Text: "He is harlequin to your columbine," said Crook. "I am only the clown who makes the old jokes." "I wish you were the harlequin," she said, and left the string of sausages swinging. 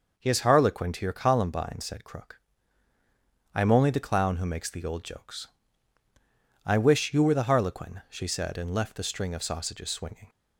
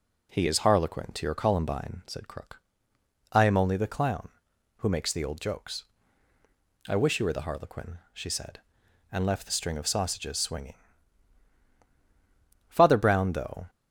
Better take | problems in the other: first | goes on to say "Father Brown though"; noticeable; from 12.6 s on; 1.0 s long

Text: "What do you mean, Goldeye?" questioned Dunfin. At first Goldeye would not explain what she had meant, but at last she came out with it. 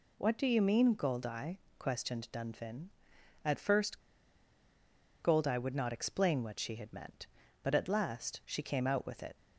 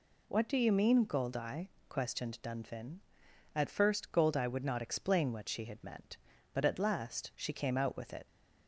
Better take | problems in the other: second | pauses between "first" and "Goldeye"; at 4.0 s; 1.2 s long

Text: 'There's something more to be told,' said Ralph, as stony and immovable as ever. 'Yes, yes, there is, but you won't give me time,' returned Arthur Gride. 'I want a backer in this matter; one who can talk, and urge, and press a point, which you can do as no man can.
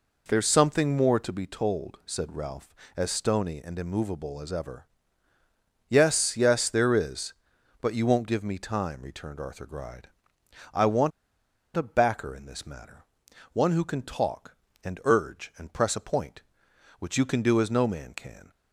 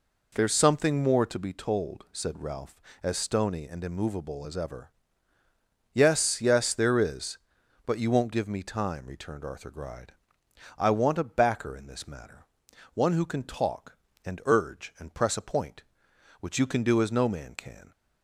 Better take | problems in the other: second | pauses between "want" and "a"; noticeable; at 11.1 s; 0.65 s long

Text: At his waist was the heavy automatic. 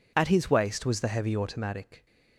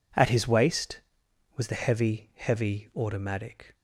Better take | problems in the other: first | says "heavy" twice; at 2.3 s

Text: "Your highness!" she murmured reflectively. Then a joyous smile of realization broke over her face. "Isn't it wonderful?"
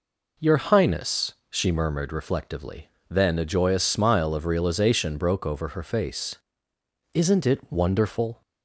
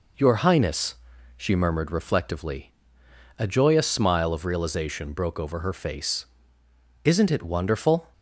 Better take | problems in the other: first | skips "Then"; at 3.0 s

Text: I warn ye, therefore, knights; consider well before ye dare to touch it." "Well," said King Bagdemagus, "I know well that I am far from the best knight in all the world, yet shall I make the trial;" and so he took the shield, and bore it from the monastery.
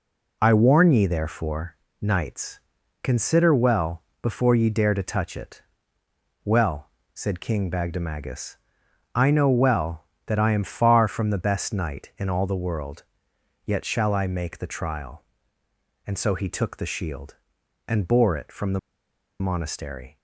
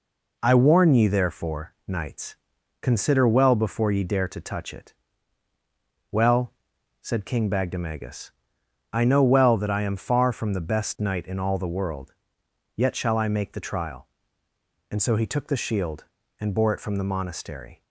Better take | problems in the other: second | pauses between "well" and "before"; slight; at 4.0 s; 0.20 s long // pauses between "the" and "monastery"; noticeable; at 18.7 s; 0.61 s long

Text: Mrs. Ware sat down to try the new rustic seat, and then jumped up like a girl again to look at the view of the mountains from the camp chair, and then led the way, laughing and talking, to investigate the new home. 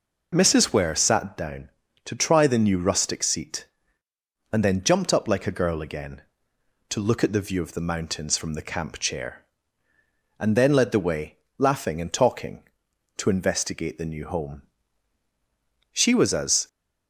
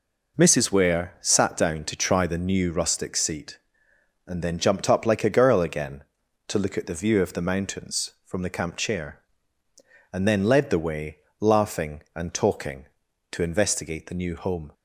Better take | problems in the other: second | goes on to say "She was as"; noticeable; from 15.9 s on; 0.76 s long

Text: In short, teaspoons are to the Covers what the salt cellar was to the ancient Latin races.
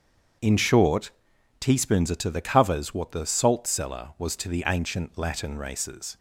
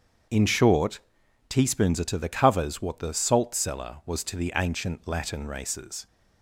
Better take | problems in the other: neither | starts louder than the rest; strong; the same in both

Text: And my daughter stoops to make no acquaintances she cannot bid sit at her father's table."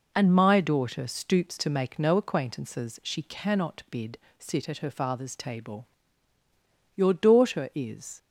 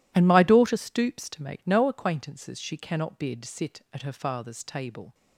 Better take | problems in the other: second | pauses between "bid" and "sit"; slight; at 4.1 s; 0.20 s long // goes on to say "Your daughter is"; noticeable; from 6.9 s on; 1.2 s long

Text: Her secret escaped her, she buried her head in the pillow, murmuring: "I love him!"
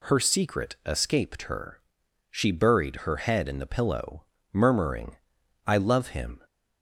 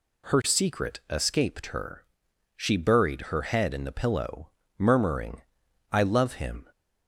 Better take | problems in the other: neither | none

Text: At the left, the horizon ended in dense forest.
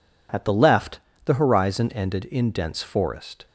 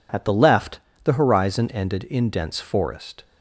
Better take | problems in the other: neither | none

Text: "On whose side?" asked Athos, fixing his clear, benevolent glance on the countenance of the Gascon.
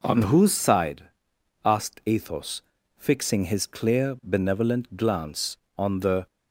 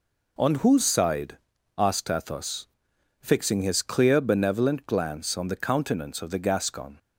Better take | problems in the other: second | stops before "countenance of the Gascon"; at 6.2 s

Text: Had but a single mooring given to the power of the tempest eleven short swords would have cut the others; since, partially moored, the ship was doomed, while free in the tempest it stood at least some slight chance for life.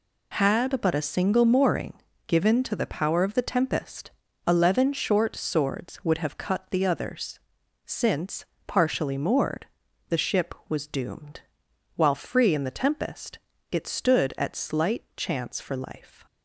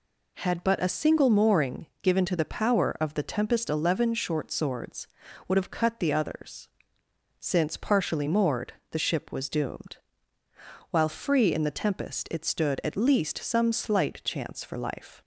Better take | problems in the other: second | pauses between "mooring" and "given"; slight; at 1.9 s; 0.34 s long; slight in the second // pauses between "tempest" and "eleven"; slight; at 4.1 s; 0.34 s long // pauses between "tempest" and "it"; slight; at 13.3 s; 0.32 s long // skips "least some"; at 14.5 s

